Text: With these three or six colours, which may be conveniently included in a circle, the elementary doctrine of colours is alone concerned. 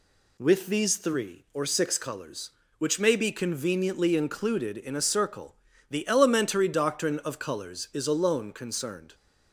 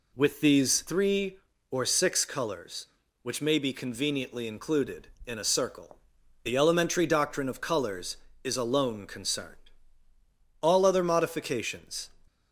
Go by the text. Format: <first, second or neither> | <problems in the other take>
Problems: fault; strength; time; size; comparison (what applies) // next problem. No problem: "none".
first | goes on to say "All other modifications"; from 10.6 s on; 1.4 s long